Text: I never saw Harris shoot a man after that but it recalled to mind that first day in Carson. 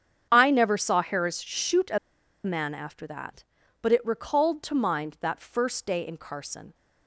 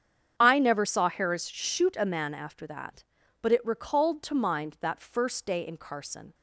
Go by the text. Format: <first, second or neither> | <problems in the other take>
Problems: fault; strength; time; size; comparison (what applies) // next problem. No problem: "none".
second | starts louder than the rest; strong; until 1.3 s; 8 dB; strong in the second // pauses between "a" and "man"; noticeable; at 1.9 s; 0.47 s long